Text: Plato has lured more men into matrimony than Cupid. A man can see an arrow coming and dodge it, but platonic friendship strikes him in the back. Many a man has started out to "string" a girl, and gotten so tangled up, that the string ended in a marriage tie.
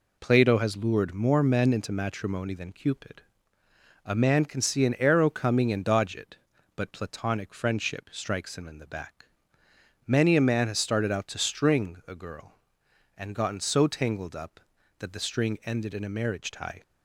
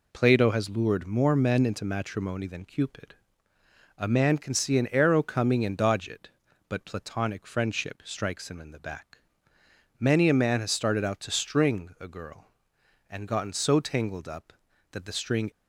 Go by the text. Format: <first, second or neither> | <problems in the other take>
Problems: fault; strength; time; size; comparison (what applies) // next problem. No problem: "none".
first | stops before "ended in a marriage tie"; at 15.5 s